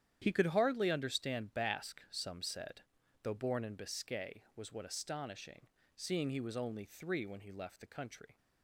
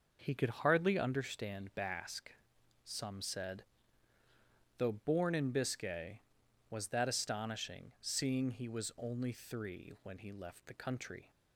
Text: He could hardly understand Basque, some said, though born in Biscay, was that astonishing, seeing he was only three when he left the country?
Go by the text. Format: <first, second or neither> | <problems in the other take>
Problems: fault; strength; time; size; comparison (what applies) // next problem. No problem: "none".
second | starts louder than the rest; strong; until 1.2 s; 10 dB // says "what" for "that"; at 4.7 s